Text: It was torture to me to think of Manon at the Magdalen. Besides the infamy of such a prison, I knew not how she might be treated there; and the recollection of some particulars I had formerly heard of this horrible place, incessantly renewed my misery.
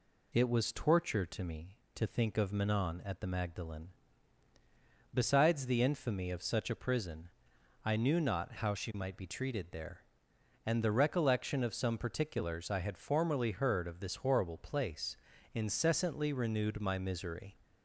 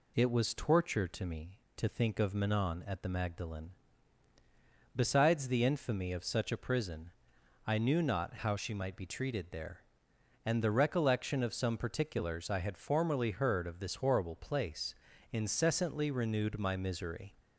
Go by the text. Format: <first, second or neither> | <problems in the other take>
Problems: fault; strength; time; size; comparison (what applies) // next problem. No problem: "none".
neither | none